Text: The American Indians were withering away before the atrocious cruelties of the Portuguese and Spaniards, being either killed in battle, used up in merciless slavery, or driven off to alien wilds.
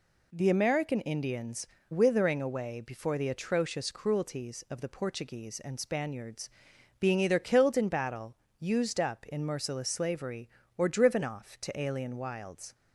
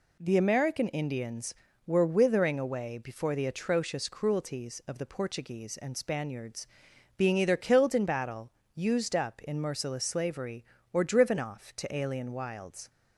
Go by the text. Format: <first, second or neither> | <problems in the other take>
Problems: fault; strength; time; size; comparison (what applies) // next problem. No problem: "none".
second | skips "were"; at 1.7 s